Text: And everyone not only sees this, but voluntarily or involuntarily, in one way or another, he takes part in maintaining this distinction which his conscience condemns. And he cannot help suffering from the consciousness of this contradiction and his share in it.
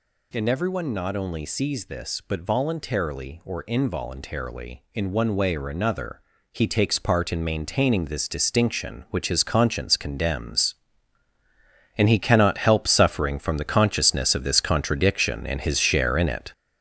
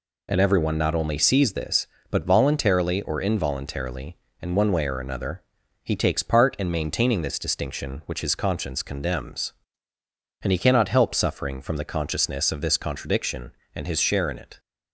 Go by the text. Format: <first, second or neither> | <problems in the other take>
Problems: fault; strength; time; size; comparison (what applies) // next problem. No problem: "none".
second | gets louder; strong; throughout; 7.5 dB